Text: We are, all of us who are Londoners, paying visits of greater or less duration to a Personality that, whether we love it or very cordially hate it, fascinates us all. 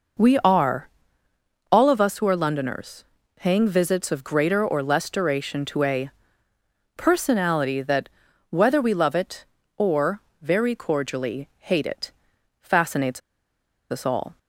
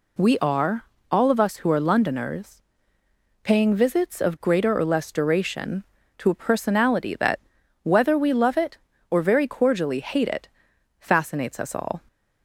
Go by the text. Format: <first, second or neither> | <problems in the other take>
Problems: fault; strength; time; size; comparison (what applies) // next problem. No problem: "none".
second | pauses between "a" and "Personality"; noticeable; at 6.0 s; 0.86 s long // pauses between "or" and "very"; slight; at 10.1 s; 0.22 s long // pauses between "fascinates" and "us"; noticeable; at 13.2 s; 0.71 s long